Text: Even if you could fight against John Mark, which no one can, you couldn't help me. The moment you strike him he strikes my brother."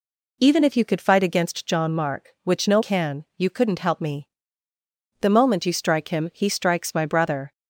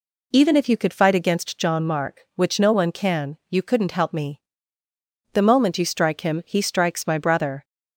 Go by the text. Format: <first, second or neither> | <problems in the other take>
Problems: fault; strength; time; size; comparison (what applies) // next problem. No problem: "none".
second | skips "one"; at 2.8 s